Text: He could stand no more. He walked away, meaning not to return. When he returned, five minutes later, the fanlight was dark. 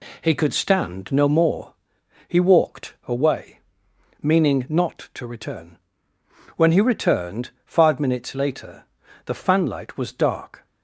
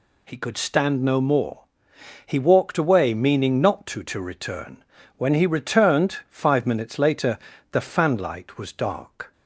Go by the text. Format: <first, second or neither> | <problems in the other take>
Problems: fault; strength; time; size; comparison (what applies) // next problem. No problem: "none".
first | says "to" twice; at 4.0 s